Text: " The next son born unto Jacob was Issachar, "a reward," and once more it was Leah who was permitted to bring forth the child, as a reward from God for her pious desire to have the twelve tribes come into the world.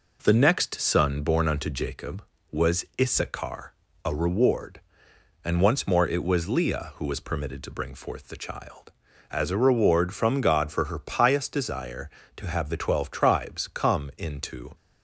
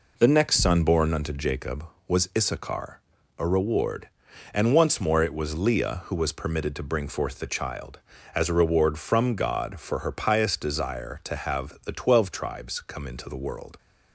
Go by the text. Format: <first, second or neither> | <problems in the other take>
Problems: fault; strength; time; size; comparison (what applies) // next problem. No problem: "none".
second | pauses between "was" and "Issachar"; slight; at 2.8 s; 0.16 s long // stops before "the world"; at 14.7 s